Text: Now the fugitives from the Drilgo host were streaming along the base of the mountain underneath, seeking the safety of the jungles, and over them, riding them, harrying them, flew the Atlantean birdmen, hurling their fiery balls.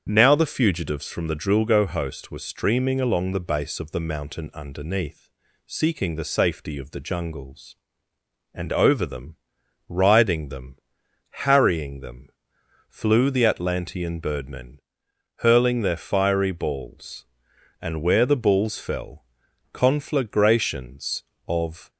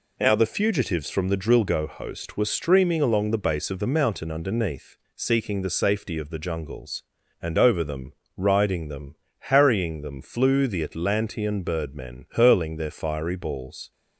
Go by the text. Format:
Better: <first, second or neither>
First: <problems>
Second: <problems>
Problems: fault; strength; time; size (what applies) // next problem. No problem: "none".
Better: second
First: starts louder than the rest; strong; until 1.1 s; 7.5 dB // goes on to say "And where the balls fell conflagrations of"; strong; from 17.8 s on; 4.0 s long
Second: none